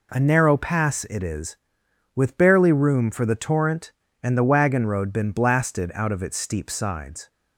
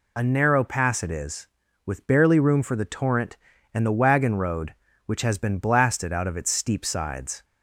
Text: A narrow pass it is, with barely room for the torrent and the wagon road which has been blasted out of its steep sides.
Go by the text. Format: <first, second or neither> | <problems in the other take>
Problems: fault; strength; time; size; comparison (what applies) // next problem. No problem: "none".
second | skips "which has"; at 5.1 s